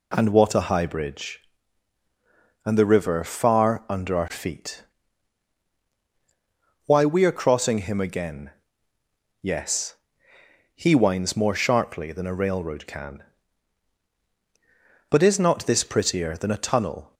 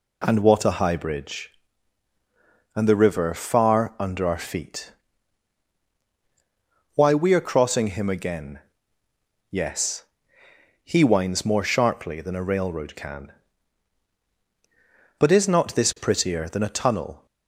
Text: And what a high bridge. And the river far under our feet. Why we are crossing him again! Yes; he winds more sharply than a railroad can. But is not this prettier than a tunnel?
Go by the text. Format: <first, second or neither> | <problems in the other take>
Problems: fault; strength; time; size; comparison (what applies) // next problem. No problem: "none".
neither | none